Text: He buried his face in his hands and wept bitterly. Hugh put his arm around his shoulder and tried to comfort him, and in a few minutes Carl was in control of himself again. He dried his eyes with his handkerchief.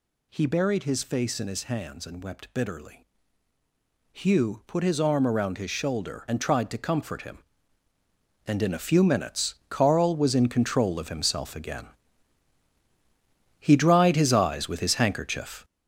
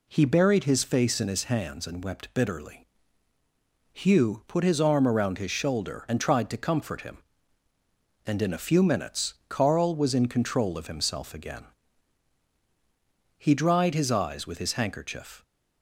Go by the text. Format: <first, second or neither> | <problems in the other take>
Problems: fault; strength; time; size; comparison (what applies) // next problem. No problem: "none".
second | gets louder; strong; throughout; 8.5 dB // pauses between "minutes" and "Carl"; slight; at 9.5 s; 0.16 s long; slight in the second